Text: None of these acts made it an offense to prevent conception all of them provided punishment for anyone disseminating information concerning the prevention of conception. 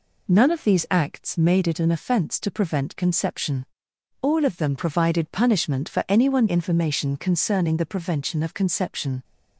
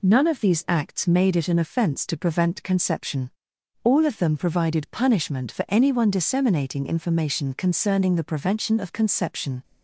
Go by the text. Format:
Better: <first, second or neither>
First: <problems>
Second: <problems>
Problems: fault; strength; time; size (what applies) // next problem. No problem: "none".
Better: second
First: pauses between "conception" and "all"; noticeable; at 3.6 s; 0.56 s long // skips "disseminating"; at 6.4 s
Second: pauses between "conception" and "all"; noticeable; at 3.3 s; 0.52 s long